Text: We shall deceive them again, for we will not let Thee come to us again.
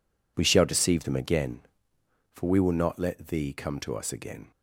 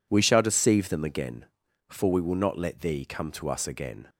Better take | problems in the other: neither | none

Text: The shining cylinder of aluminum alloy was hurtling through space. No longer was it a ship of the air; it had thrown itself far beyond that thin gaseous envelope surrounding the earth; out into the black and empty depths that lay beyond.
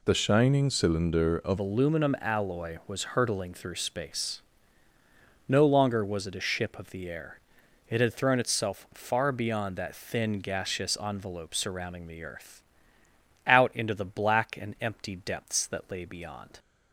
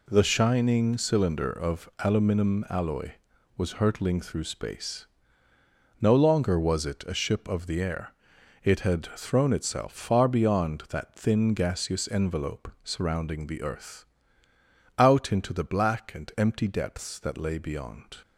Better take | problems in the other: second | changes voice at "aluminum"; from 1.5 s on; 15.0 s long

